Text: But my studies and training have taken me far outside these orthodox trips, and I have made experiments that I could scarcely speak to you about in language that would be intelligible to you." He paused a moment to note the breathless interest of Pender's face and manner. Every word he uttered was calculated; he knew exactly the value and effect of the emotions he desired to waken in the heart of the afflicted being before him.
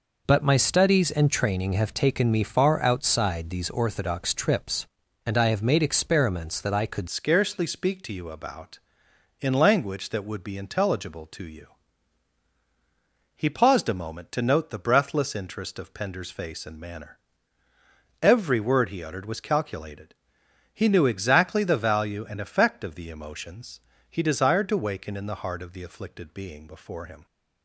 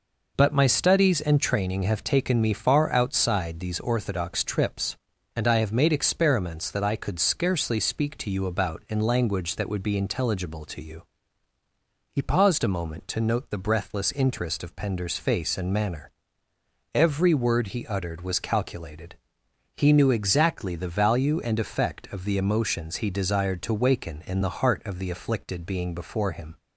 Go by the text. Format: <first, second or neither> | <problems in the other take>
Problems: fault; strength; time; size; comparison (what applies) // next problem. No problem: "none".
second | changes voice at "scarcely"; from 7.0 s on; 20.2 s long // pauses between "emotions" and "he"; slight; at 23.8 s; 0.28 s long